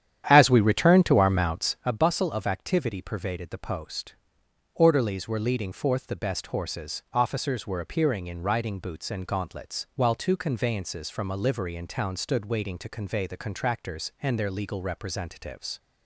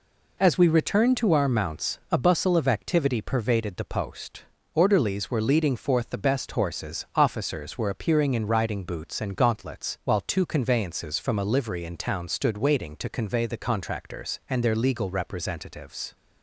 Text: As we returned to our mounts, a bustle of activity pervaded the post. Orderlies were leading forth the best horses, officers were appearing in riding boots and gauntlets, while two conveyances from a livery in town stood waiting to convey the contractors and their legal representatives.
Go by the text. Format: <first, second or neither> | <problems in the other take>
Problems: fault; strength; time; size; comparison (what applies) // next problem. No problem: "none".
second | starts louder than the rest; strong; until 1.9 s; 10 dB